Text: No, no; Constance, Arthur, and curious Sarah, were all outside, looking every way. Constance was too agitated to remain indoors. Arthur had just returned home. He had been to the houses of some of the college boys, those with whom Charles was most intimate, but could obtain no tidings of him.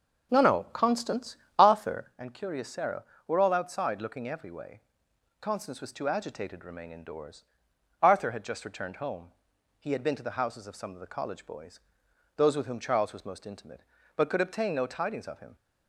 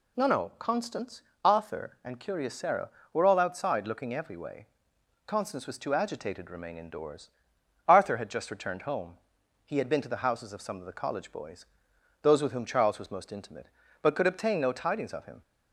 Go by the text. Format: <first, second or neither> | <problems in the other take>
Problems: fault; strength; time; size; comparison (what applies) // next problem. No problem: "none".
second | starts louder than the rest; strong; until 2.2 s; 8 dB